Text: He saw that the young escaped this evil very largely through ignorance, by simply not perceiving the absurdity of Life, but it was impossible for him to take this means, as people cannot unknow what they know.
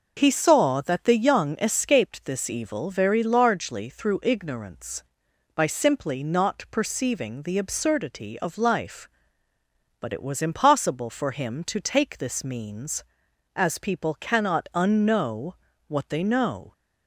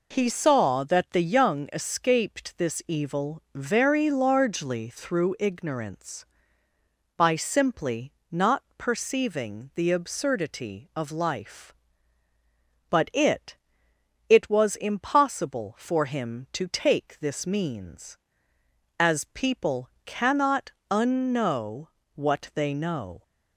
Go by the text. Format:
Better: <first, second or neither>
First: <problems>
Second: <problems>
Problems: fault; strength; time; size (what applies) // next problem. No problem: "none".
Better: first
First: pauses between "unknow" and "what"; slight; at 15.5 s; 0.36 s long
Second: pauses between "simply" and "not"; slight; at 8.1 s; 0.18 s long // says "it" twice; at 14.2 s // pauses between "people" and "cannot"; slight; at 19.8 s; 0.16 s long // pauses between "cannot" and "unknow"; slight; at 20.7 s; 0.20 s long // pauses between "unknow" and "what"; slight; at 21.8 s; 0.29 s long